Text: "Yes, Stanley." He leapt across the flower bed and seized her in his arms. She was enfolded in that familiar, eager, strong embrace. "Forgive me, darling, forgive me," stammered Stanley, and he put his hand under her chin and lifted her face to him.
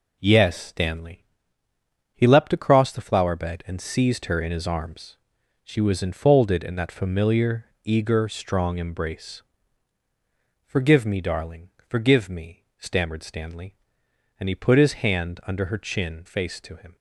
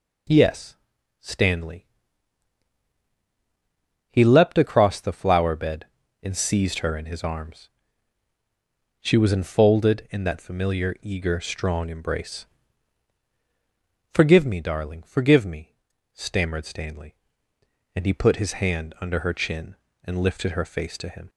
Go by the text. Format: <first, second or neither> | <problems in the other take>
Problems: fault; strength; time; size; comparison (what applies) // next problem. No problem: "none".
second | skips "and lifted her"; at 16.2 s